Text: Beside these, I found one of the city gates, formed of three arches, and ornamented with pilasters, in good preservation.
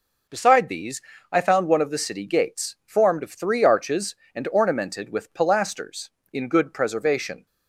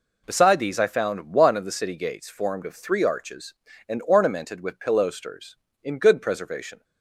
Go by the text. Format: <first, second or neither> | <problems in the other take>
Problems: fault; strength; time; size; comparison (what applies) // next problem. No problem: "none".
neither | none